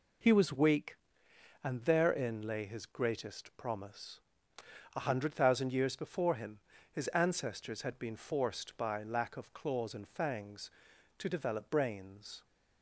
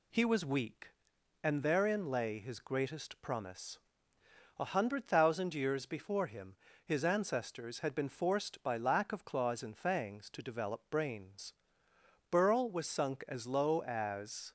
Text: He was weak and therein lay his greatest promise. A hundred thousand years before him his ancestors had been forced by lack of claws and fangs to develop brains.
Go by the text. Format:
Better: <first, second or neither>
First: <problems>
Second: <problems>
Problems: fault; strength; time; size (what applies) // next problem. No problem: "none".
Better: first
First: pauses between "him" and "his"; slight; at 6.5 s; 0.32 s long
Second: pauses between "him" and "his"; slight; at 6.5 s; 0.28 s long // goes on to say "Burl was sunk as low as"; strong; from 12.2 s on; 2.2 s long